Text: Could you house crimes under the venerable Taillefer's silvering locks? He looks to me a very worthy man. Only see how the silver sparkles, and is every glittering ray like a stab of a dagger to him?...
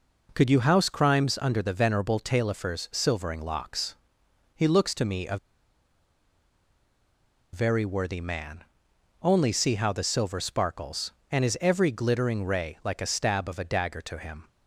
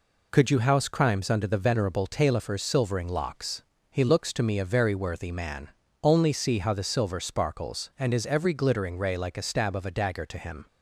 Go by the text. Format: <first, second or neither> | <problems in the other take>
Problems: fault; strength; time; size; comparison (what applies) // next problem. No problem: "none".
second | pauses between "a" and "very"; strong; at 5.3 s; 2.1 s long